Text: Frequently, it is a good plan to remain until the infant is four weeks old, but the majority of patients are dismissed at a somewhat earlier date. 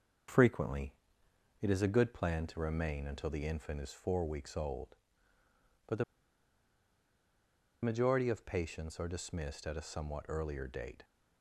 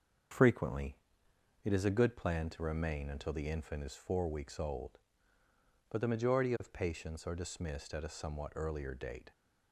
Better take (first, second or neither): second